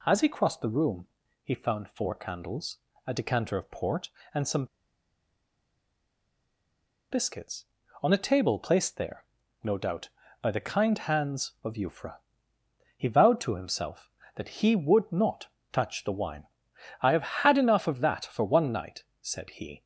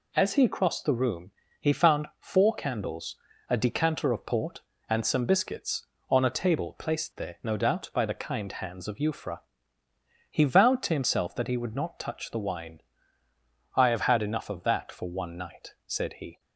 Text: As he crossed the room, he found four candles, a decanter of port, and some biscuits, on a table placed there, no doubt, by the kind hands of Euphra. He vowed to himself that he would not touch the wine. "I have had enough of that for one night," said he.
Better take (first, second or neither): second